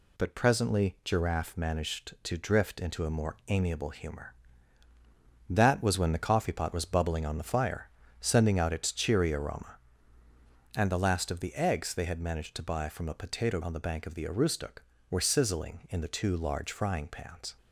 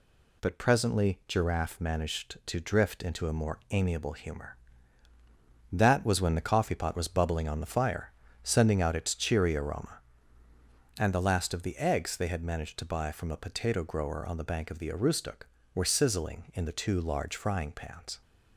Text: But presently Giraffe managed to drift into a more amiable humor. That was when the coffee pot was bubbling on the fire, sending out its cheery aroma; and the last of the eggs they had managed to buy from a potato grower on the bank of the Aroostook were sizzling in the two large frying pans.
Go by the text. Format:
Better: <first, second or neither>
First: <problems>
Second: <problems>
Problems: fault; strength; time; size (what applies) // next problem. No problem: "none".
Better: second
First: skips "grower"; at 13.6 s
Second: none